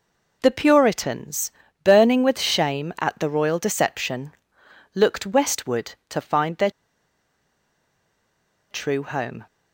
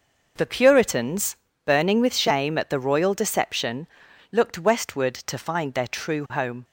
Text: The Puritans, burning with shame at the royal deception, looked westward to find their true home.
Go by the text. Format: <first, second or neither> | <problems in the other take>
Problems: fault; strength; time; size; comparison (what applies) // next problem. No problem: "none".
second | pauses between "their" and "true"; strong; at 6.6 s; 2.0 s long